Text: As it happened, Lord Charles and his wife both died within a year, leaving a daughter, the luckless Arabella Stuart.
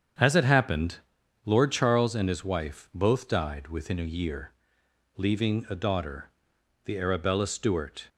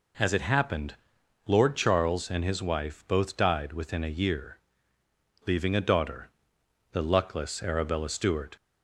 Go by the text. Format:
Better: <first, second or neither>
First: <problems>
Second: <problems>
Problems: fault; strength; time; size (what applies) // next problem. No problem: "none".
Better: second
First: starts louder than the rest; strong; until 1.6 s; 8 dB // skips "luckless"; at 6.9 s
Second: none